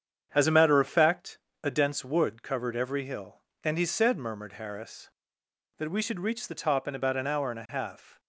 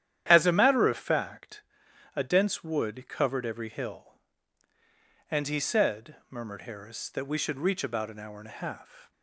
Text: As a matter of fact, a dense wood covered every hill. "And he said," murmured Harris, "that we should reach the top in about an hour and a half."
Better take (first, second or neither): first